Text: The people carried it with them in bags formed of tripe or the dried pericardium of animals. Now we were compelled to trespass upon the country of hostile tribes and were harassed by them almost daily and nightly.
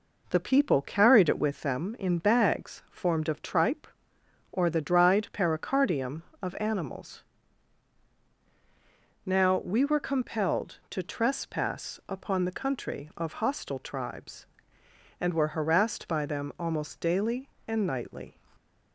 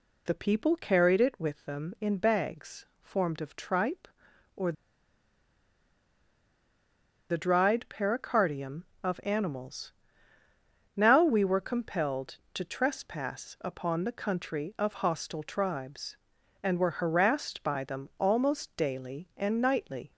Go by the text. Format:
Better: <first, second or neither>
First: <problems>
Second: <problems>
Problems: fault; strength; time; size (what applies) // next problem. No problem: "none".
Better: first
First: none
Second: pauses between "bags" and "formed"; slight; at 2.8 s; 0.16 s long // pauses between "or" and "the"; strong; at 4.7 s; 2.5 s long